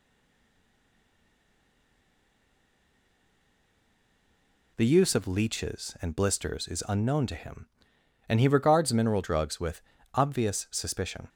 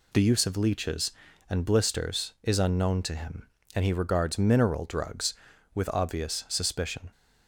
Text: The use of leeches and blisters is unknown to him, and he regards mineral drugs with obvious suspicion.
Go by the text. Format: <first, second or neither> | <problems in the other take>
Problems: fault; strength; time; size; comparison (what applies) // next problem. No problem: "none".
second | stays silent before the first word; strong; until 4.7 s; 4.7 s long // pauses between "with" and "obvious"; slight; at 9.8 s; 0.32 s long